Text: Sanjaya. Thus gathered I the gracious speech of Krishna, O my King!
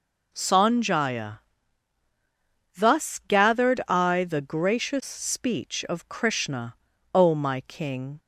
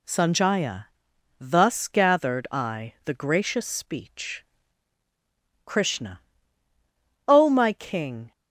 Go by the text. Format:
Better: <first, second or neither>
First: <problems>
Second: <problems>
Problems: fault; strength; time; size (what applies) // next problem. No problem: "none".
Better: first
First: none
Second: skips "of"; at 5.0 s